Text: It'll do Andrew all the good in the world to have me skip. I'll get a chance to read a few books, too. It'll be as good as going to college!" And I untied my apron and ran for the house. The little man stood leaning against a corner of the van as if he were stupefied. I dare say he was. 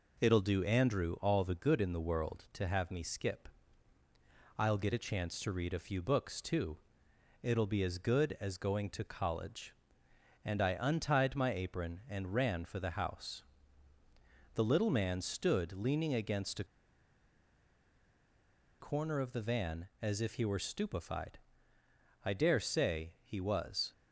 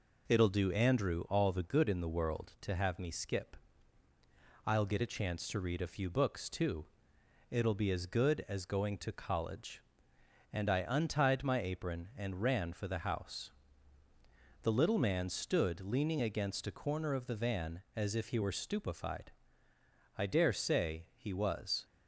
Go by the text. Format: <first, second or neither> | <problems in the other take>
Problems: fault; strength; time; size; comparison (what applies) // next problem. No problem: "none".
second | pauses between "a" and "corner"; strong; at 16.6 s; 2.1 s long